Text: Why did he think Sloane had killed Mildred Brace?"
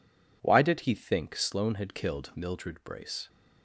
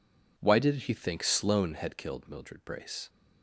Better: neither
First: none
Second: none

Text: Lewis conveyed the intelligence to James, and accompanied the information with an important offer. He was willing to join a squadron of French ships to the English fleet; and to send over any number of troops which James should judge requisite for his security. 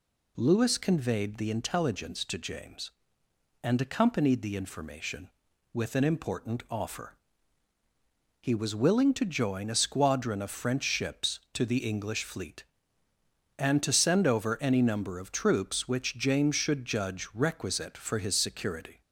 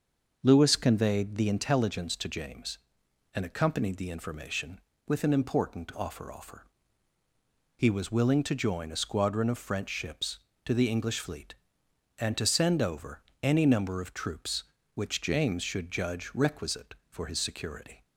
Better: first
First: none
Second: starts louder than the rest; until 1.4 s; 6.5 dB // says "offer" twice; at 6.3 s // pauses between "over" and "any"; slight; at 13.2 s; 0.22 s long

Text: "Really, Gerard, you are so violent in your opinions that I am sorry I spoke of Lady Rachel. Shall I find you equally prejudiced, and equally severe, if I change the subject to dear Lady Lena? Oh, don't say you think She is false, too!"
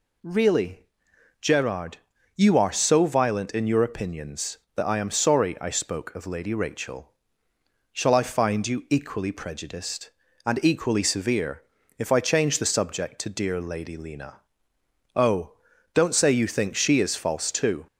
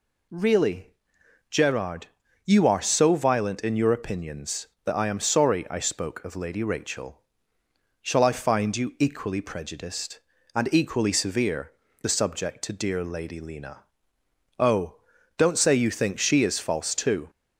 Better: first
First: none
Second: skips "if I change"; at 11.8 s

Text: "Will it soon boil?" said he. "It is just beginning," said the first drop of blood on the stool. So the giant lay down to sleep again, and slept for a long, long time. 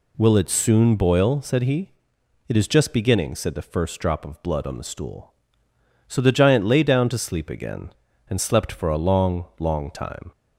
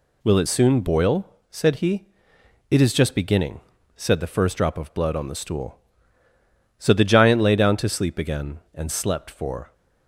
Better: first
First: none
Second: stops before "a long long time"; at 9.7 s

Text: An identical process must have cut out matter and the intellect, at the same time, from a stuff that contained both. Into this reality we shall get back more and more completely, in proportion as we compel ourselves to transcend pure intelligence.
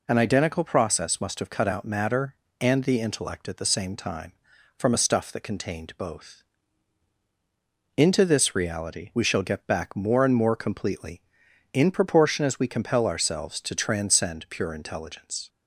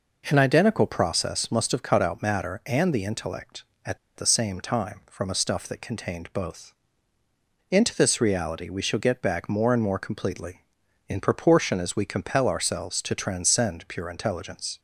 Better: first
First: none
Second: pauses between "at" and "the"; slight; at 3.9 s; 0.19 s long

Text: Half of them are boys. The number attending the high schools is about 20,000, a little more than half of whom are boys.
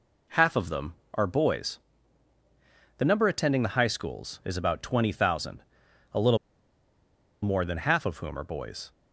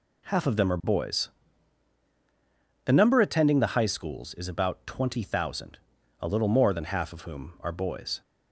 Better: second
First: pauses between "little" and "more"; at 6.3 s; 1.0 s long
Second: none

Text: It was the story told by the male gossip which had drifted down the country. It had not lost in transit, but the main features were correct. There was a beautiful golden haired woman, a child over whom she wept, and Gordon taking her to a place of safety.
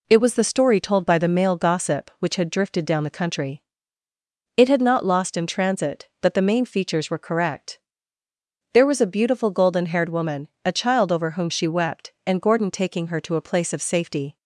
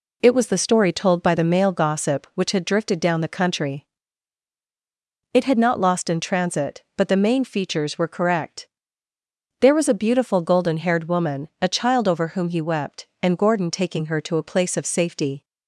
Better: first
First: none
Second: says "he" for "she"; at 12.5 s

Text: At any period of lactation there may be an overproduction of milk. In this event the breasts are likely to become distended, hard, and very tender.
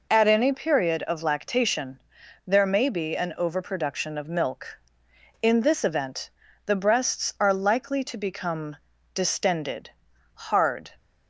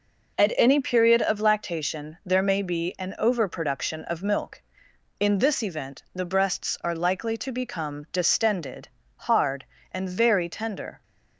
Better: second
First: pauses between "lactation" and "there"; noticeable; at 1.9 s; 0.46 s long // pauses between "event" and "the"; at 6.2 s; 0.38 s long // pauses between "become" and "distended"; at 8.7 s; 0.38 s long // stops before "and very tender"; at 10.9 s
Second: none

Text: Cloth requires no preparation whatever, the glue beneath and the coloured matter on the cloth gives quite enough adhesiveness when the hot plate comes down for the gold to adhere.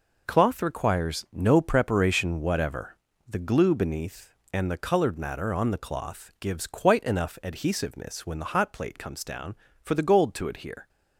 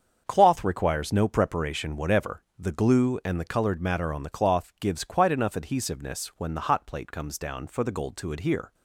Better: first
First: none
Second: starts louder than the rest; until 1.2 s; 7 dB // skips "beneath"; at 3.2 s

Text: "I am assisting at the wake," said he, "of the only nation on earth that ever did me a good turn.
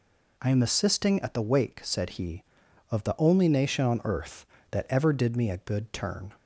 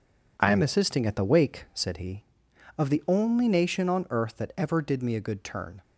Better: neither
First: none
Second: none

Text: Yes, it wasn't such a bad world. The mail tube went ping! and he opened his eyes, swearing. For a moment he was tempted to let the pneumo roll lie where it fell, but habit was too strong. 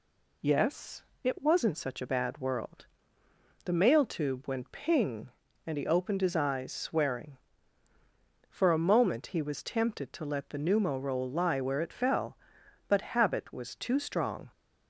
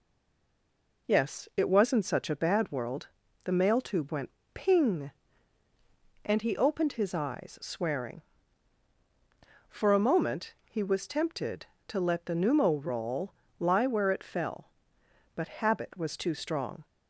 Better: first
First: none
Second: stays silent before the first word; until 1.0 s; 1.0 s long // pauses between "went" and "ping"; slight; at 4.3 s; 0.24 s long // pauses between "roll" and "lie"; slight; at 13.3 s; 0.24 s long

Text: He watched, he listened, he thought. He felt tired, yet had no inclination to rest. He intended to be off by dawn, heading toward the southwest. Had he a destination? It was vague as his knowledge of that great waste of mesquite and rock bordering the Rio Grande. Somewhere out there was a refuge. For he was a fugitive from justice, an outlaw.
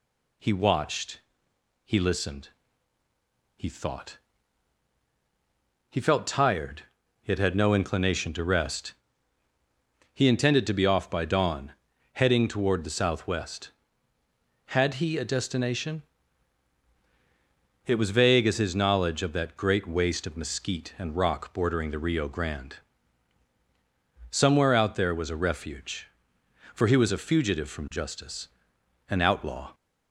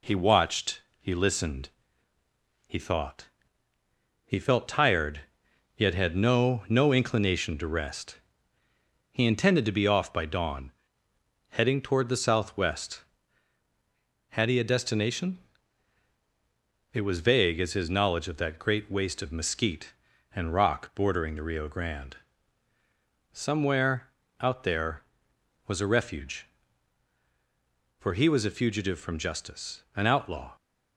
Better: first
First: none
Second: says "no" twice; at 6.6 s // pauses between "Somewhere" and "out"; slight; at 24.0 s; 0.32 s long

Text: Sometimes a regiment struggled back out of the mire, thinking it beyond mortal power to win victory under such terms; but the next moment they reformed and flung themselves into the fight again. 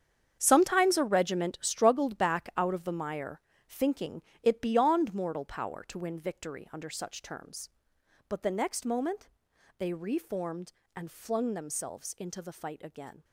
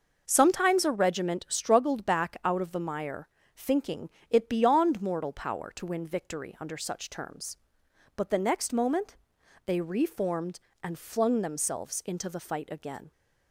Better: second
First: gets quieter; strong; throughout; 13.5 dB // pauses between "thinking" and "it"; slight; at 4.2 s; 0.22 s long // pauses between "moment" and "they"; noticeable; at 9.2 s; 0.50 s long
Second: pauses between "thinking" and "it"; slight; at 4.0 s; 0.22 s long // pauses between "moment" and "they"; noticeable; at 9.1 s; 0.50 s long

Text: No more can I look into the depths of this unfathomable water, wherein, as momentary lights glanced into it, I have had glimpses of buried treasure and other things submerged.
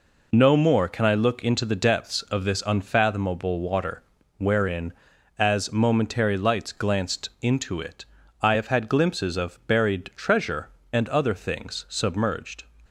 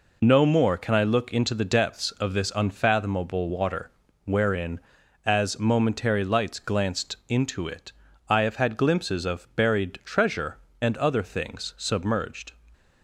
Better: neither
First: none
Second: none

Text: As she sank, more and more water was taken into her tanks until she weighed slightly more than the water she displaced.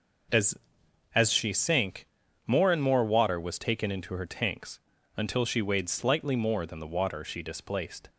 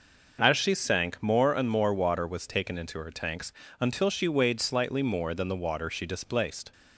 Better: second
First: says "As" twice; at 1.1 s // pauses between "tanks" and "until"; at 4.7 s; 0.38 s long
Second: pauses between "tanks" and "until"; slight; at 3.5 s; 0.26 s long

